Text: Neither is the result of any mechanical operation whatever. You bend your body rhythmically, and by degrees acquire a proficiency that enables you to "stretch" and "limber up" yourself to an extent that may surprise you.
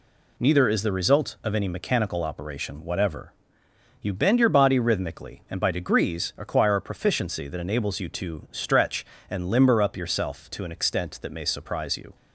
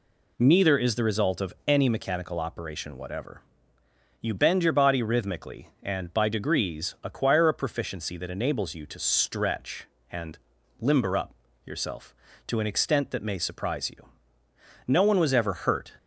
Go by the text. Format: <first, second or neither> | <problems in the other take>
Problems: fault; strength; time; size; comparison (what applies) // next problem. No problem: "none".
first | pauses between "and" and "limber"; at 10.3 s; 0.44 s long // pauses between "up" and "yourself"; slight; at 11.3 s; 0.32 s long // goes on to say "No one was ever hurt"; noticeable; from 14.8 s on; 1.0 s long